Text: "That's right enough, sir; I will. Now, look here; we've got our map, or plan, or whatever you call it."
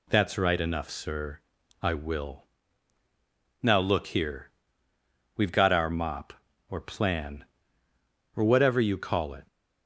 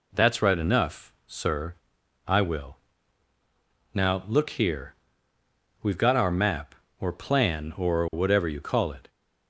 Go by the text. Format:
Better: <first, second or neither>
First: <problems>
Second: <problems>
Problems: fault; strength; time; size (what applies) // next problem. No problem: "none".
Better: second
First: says "mop" for "map"; at 5.8 s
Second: none